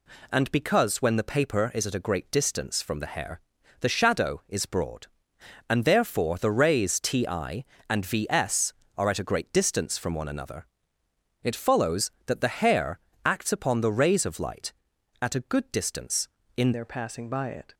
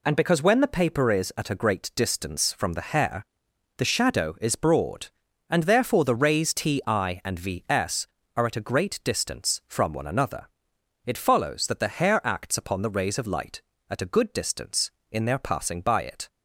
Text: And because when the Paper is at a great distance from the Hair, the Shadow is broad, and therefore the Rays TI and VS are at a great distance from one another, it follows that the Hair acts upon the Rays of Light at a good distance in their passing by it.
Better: second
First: pauses between "Hair" and "acts"; slight; at 12.9 s; 0.26 s long // changes voice at "their"; from 16.7 s on; 1.0 s long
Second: none

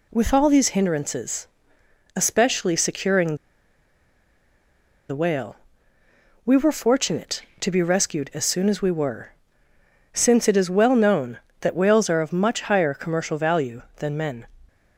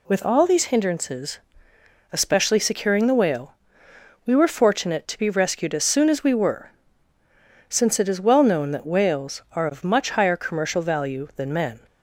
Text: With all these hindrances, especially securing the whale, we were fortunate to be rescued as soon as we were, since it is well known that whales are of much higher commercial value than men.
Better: second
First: pauses between "securing" and "the"; strong; at 3.3 s; 1.7 s long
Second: none

